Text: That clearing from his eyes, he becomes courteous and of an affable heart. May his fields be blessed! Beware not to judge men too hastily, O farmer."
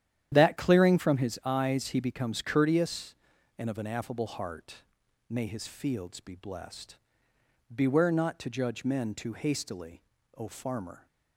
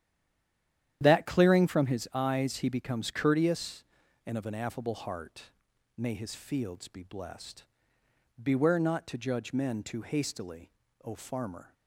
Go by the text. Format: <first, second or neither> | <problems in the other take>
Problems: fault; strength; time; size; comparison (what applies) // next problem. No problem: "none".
first | stays silent before the first word; until 1.0 s; 1.0 s long // starts louder than the rest; strong; until 2.0 s; 10.5 dB; strong in the first